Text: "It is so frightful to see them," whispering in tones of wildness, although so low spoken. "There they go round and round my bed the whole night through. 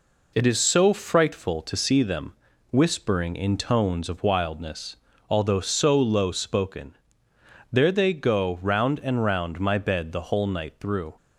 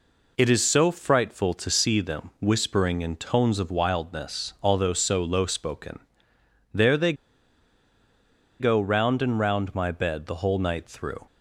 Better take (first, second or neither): first